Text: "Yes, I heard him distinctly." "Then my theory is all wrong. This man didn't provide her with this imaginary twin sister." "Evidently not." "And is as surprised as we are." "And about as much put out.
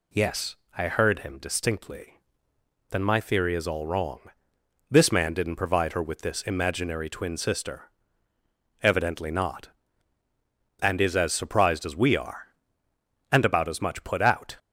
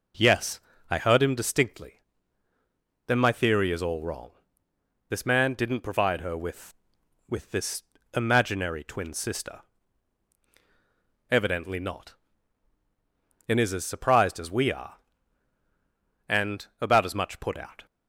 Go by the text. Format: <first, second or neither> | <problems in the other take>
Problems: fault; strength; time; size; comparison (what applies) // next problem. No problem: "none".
first | says "with" twice; at 7.2 s // pauses between "this" and "imaginary"; slight; at 7.8 s; 0.30 s long